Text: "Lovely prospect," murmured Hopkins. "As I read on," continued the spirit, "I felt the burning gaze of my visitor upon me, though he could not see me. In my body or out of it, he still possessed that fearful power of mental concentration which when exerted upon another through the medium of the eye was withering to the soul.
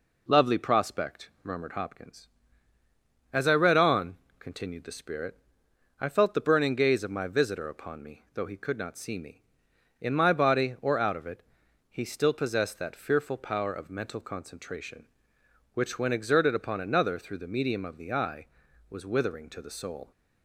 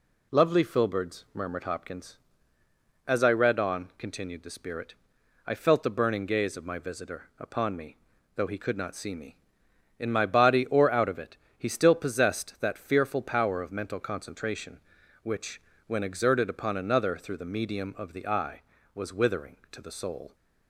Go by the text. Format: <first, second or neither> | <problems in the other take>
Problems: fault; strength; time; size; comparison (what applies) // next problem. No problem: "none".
first | says "filberds" for "prospect"; at 0.6 s // pauses between "which" and "when"; slight; at 15.6 s; 0.24 s long